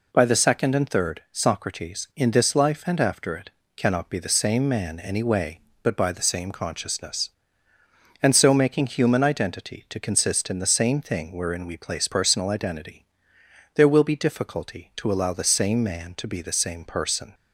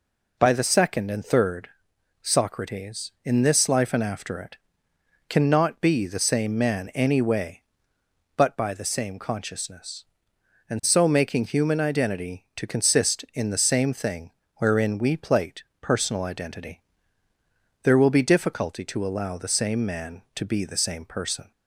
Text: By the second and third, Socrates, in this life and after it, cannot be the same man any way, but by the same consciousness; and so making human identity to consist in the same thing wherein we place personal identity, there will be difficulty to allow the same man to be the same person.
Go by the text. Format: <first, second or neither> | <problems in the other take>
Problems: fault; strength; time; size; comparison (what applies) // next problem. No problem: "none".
first | pauses between "thing" and "wherein"; slight; at 14.3 s; 0.24 s long // says "plate" for "place"; at 15.1 s